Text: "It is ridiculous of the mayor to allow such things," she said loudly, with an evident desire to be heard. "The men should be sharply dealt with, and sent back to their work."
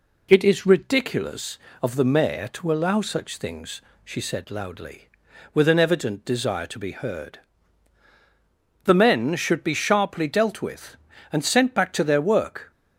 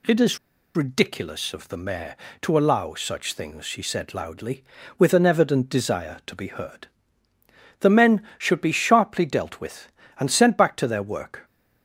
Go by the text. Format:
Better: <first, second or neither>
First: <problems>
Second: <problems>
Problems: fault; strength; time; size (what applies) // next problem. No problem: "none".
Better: first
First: none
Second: pauses between "is" and "ridiculous"; at 0.3 s; 0.37 s long